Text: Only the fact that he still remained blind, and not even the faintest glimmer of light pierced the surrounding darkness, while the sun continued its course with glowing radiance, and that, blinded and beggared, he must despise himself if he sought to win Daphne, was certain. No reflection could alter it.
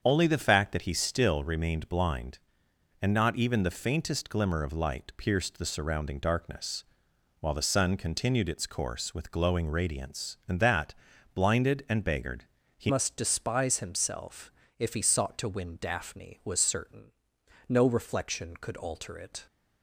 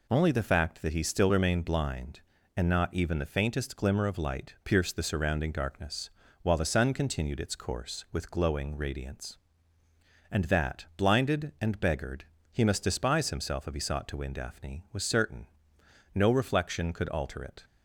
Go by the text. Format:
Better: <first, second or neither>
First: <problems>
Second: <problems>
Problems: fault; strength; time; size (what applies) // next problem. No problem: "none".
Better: second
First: starts louder than the rest; strong; until 1.0 s; 7.5 dB // changes voice at "must"; from 12.8 s on; 6.6 s long // pauses between "himself" and "if"; slight; at 14.5 s; 0.28 s long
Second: none